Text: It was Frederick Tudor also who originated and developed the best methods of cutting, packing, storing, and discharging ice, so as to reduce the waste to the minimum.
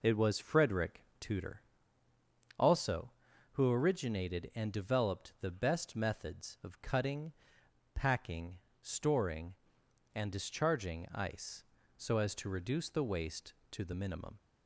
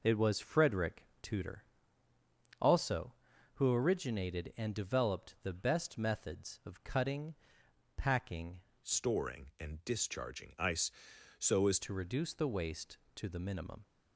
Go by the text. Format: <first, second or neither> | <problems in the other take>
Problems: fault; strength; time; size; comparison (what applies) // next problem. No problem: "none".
first | pauses between "Frederick" and "Tudor"; slight; at 1.0 s; 0.16 s long; slight in the first // pauses between "Tudor" and "also"; noticeable; at 1.6 s; 0.96 s long; noticeable in the first // changes voice from "storing" to "as"; from 8.8 to 11.7 s; 2.9 s long